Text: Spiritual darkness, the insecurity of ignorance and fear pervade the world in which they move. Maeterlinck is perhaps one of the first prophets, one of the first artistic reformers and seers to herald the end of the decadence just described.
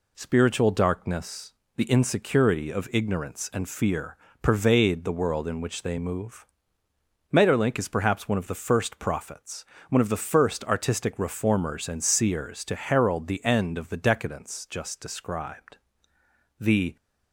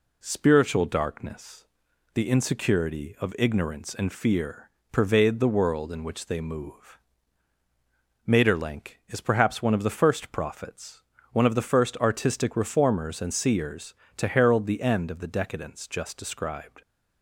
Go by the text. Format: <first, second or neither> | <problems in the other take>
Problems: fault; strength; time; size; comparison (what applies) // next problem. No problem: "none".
second | pauses between "fear" and "pervade"; slight; at 4.1 s; 0.24 s long; slight in the second // goes on to say "The"; slight; from 16.5 s on; 0.36 s long